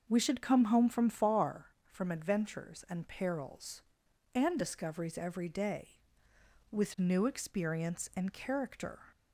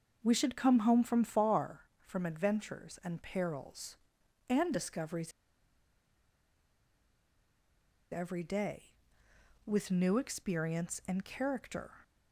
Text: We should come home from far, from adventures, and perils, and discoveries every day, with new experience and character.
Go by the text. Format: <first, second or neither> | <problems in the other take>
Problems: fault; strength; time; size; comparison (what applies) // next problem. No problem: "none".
first | starts louder than the rest; until 1.2 s; 6 dB; also in the first // pauses between "discoveries" and "every"; strong; at 5.3 s; 2.8 s long